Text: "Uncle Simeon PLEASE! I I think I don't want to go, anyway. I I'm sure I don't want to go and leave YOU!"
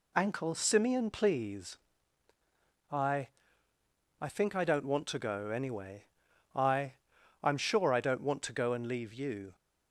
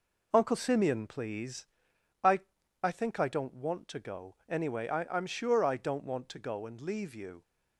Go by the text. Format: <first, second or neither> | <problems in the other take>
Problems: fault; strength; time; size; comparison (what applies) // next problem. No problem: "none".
second | says "Ankle" for "Uncle"; at 0.1 s // pauses between "I" and "I"; noticeable; at 3.2 s; 0.92 s long; also in the second // pauses between "I" and "I'm"; noticeable; at 6.9 s; 0.50 s long